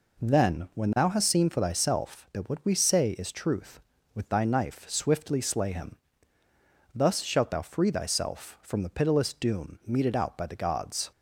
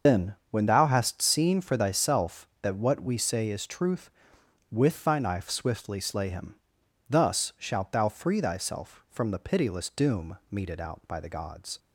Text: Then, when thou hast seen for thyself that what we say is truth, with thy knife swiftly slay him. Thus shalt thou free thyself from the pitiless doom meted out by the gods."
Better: first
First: none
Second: loses the start of "Then"; at 0.0 s; 65 ms // starts louder than the rest; until 1.2 s; 6 dB

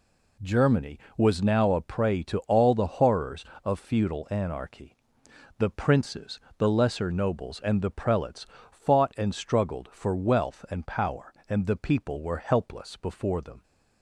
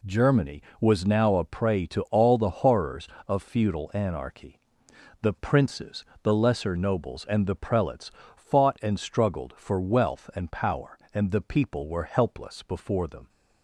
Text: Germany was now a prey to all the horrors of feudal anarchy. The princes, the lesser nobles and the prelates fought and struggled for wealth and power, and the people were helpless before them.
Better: neither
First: pauses between "prelates" and "fought"; slight; at 8.4 s; 0.24 s long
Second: pauses between "prelates" and "fought"; slight; at 8.1 s; 0.24 s long

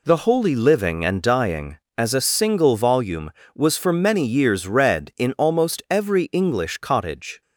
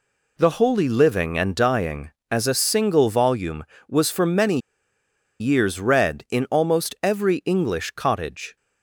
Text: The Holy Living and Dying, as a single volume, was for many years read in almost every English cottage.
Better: first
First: none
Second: pauses between "many" and "years"; noticeable; at 4.5 s; 0.81 s long

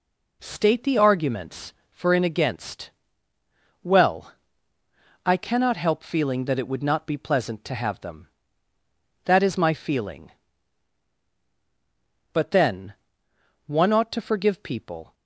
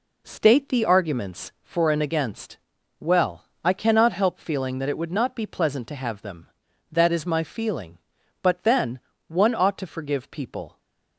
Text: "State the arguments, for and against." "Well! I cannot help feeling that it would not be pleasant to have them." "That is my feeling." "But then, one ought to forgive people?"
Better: neither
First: none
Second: none

